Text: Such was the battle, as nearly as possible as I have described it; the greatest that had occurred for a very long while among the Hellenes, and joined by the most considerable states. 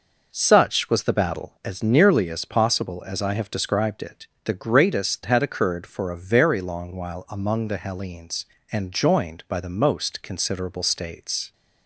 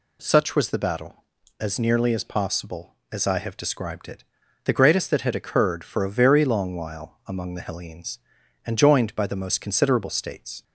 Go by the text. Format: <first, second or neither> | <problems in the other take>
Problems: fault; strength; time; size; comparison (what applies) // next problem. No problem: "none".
second | skips "that"; at 5.2 s